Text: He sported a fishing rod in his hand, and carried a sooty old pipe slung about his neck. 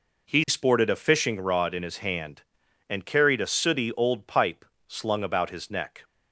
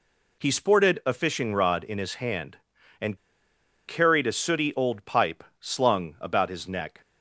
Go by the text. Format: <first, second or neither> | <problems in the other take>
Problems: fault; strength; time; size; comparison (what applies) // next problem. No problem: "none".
first | pauses between "and" and "carried"; noticeable; at 3.1 s; 0.69 s long // pauses between "pipe" and "slung"; slight; at 5.4 s; 0.18 s long; slight in the first